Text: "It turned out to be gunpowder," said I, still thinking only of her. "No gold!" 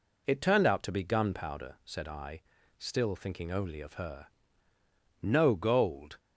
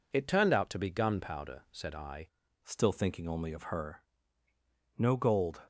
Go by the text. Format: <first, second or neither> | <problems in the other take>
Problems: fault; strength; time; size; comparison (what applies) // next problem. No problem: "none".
first | changes voice at "still"; from 2.6 s on; 3.0 s long